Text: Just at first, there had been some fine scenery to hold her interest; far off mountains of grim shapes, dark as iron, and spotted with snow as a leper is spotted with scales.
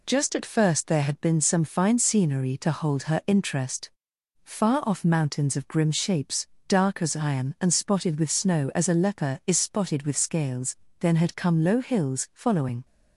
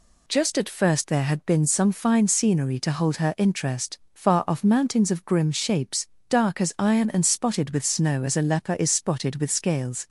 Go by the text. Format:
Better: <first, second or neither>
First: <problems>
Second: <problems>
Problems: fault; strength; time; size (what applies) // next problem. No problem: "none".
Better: second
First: goes on to say "Then had come low hills following"; strong; from 10.9 s on; 1.8 s long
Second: none